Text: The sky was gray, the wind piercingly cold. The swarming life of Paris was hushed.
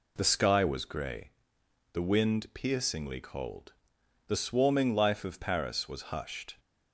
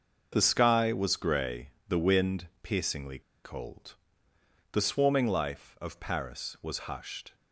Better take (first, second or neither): first